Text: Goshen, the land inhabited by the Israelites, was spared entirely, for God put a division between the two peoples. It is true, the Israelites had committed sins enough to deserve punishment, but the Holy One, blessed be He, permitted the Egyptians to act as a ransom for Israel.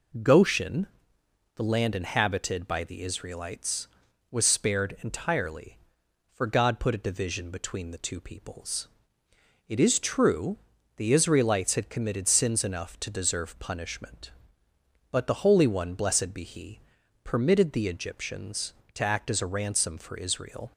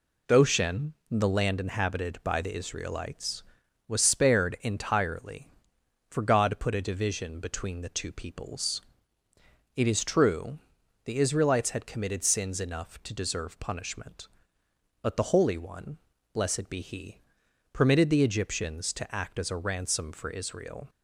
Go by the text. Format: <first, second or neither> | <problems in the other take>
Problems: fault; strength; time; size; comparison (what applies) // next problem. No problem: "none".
neither | none